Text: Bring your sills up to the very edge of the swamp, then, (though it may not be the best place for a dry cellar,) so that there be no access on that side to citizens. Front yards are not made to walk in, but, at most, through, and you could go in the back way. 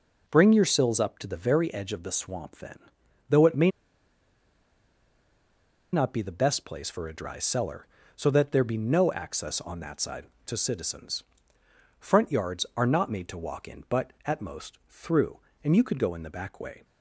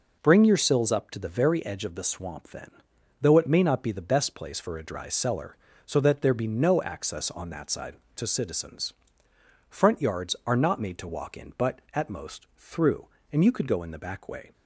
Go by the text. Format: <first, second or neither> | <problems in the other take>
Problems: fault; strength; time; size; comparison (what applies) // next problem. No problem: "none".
second | pauses between "may" and "not"; strong; at 3.7 s; 2.2 s long